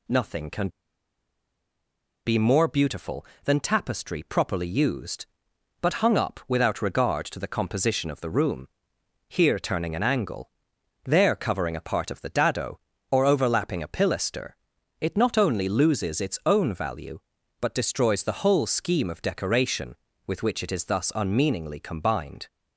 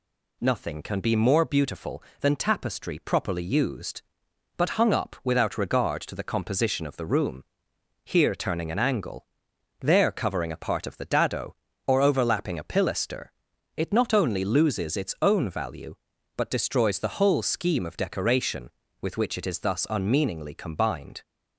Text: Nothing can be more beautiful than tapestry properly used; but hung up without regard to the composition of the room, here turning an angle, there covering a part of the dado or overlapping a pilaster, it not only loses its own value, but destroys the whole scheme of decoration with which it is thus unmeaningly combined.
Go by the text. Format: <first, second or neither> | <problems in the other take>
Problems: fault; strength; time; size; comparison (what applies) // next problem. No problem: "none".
second | pauses between "can" and "be"; strong; at 0.6 s; 1.5 s long